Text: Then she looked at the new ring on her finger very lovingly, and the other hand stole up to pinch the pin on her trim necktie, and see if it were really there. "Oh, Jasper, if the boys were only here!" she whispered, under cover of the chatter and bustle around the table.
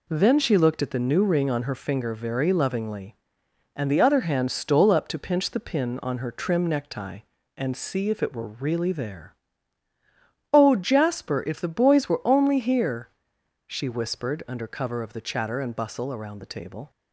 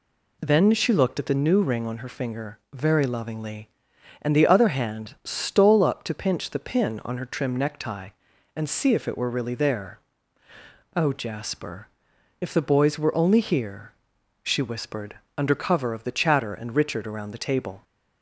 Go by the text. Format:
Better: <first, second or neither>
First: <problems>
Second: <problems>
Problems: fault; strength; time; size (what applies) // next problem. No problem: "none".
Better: first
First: none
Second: says "richard" for "bustle"; at 16.7 s